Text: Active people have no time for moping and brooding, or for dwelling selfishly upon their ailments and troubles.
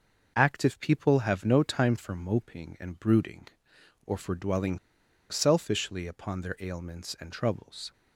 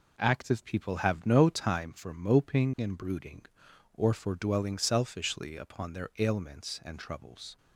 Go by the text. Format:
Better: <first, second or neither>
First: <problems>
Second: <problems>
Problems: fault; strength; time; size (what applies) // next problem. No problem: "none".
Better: second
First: pauses between "dwelling" and "selfishly"; noticeable; at 4.7 s; 0.51 s long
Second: none